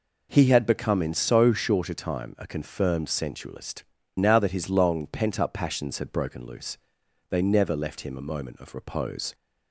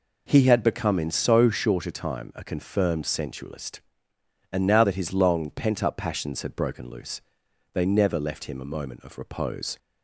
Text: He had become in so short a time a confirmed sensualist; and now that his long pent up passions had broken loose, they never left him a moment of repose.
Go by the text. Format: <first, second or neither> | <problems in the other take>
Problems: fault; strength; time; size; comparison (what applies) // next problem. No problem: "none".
second | skips "and"; at 4.0 s